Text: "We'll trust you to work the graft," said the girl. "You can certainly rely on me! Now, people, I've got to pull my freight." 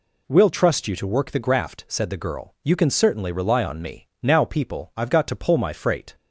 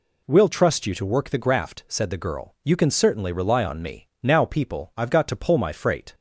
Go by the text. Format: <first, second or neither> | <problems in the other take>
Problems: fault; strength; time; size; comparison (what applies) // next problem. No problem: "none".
neither | none